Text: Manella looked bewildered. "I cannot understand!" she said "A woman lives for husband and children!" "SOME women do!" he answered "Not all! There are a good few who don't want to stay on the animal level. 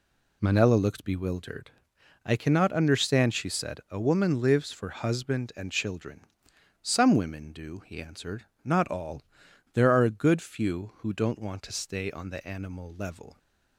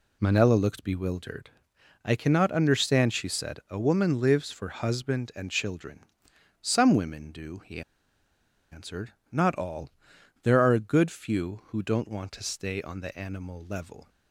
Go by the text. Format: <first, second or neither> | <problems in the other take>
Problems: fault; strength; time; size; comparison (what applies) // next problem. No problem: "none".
first | pauses between "he" and "answered"; noticeable; at 7.8 s; 0.91 s long // pauses between "answered" and "Not"; slight; at 9.1 s; 0.18 s long; slight in the first